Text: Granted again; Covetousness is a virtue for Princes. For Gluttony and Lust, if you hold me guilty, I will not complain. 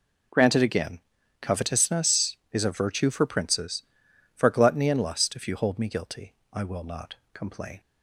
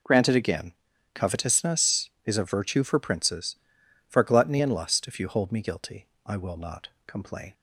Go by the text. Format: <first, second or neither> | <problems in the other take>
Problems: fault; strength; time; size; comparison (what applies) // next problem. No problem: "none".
neither | pauses between "not" and "complain"; slight; the same in both